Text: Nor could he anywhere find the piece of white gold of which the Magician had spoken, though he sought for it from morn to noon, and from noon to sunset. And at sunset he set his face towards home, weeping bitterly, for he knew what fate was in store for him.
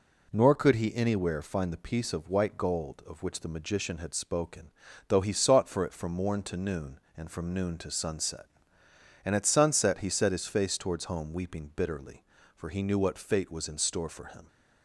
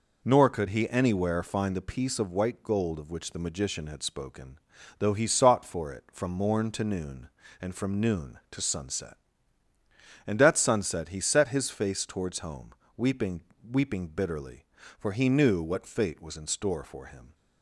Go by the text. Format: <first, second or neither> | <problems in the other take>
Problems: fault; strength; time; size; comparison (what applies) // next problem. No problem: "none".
first | says "weeping" twice; at 13.6 s